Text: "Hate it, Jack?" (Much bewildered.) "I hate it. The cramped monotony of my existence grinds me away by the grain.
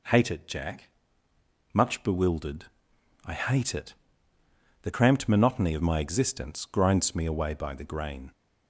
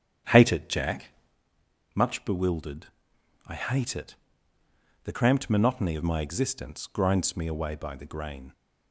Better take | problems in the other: first | starts louder than the rest; strong; until 1.3 s; 8.5 dB

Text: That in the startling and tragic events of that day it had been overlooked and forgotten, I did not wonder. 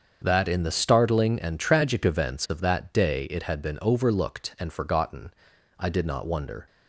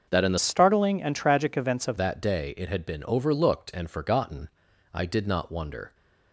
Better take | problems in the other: first | starts louder than the rest; until 1.1 s; 6.5 dB; strong in the first // changes voice from "startling" to "of"; from 0.3 to 1.9 s; 1.6 s long

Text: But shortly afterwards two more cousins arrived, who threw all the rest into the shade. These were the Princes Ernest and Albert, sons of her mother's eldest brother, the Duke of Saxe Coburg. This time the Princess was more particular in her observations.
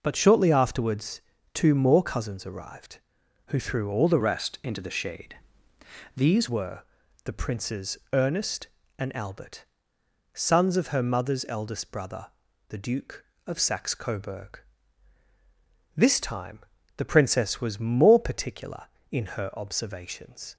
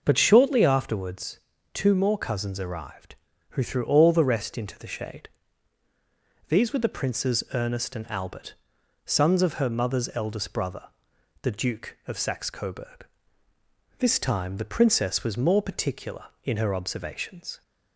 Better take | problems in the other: second | pauses between "afterwards" and "two"; slight; at 1.2 s; 0.34 s long; slight in the second // changes voice from "rest" to "These"; from 4.1 to 6.4 s; 2.3 s long // pauses between "were" and "the"; at 6.8 s; 0.44 s long // pauses between "Princes" and "Ernest"; slight; at 7.9 s; 0.16 s long // pauses between "time" and "the"; at 16.5 s; 0.38 s long

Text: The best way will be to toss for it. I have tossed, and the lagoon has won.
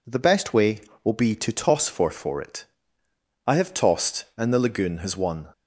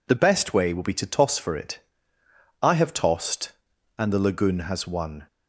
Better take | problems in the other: second | says "for" twice; at 2.0 s

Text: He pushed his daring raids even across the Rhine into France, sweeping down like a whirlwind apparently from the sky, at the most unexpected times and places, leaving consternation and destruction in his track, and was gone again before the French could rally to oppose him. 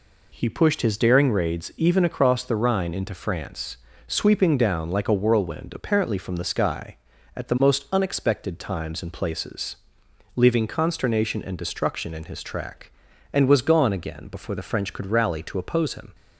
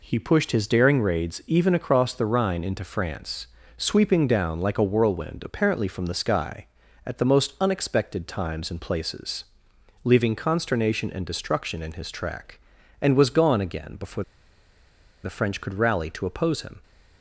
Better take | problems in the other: first | pauses between "before" and "the"; at 14.2 s; 1.0 s long

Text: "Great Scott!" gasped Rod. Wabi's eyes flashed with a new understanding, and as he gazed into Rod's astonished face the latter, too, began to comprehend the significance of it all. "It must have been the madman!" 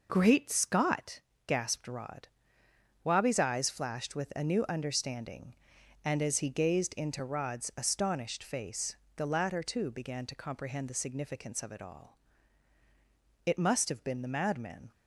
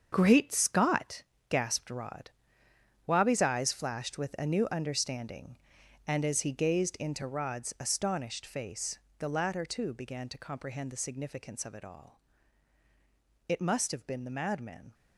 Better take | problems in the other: first | gets quieter; strong; throughout; 11 dB // pauses between "face" and "the"; slight; at 8.9 s; 0.18 s long; slight in the first

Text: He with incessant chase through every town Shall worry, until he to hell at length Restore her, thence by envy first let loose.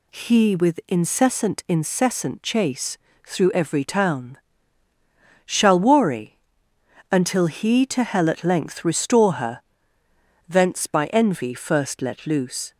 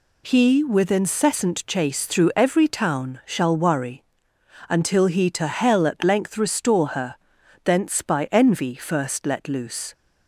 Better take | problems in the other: second | says "incessant" twice; at 1.6 s // pauses between "chase" and "through"; slight; at 2.9 s; 0.30 s long // pauses between "town" and "Shall"; at 4.3 s; 1.0 s long

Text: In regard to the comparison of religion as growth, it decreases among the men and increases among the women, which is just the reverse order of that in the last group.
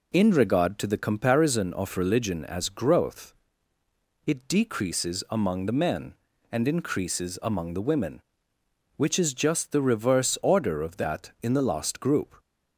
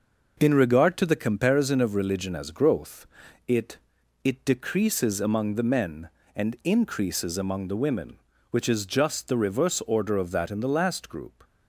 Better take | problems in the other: first | says "it" twice; at 4.2 s

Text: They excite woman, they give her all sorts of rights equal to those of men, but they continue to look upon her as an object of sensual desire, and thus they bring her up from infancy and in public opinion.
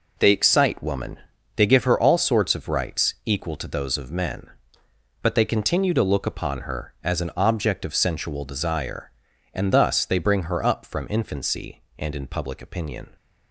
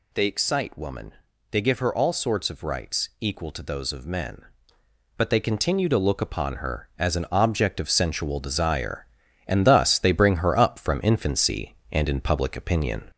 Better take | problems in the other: first | gets louder; slight; throughout; 2 dB

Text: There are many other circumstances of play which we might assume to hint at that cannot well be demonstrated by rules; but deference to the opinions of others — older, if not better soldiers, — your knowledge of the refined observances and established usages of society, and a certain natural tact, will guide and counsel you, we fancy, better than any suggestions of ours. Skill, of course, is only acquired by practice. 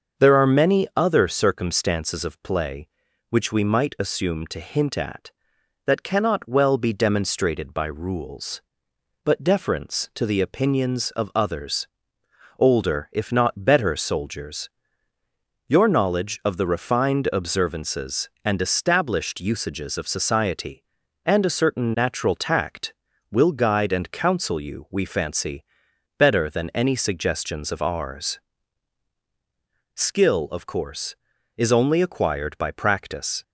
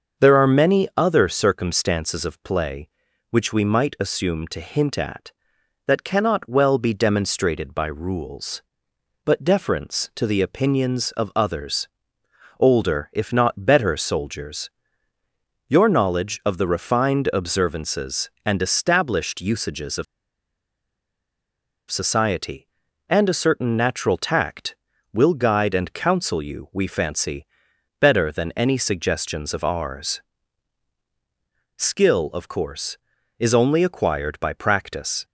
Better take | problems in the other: first | starts louder than the rest; until 1.3 s; 6.5 dB; also in the first // pauses between "of" and "society"; strong; at 20.0 s; 1.8 s long

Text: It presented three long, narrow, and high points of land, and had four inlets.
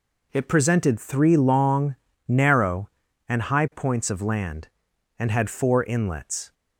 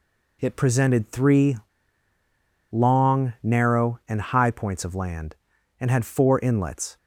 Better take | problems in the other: first | pauses between "three" and "long"; at 1.5 s; 1.1 s long

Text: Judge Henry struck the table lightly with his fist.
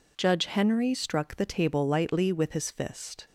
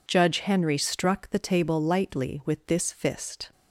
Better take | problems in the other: first | says "this" for "his"; at 2.6 s

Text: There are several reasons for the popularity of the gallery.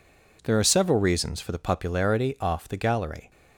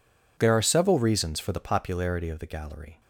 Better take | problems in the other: second | says "off" for "of"; at 2.4 s

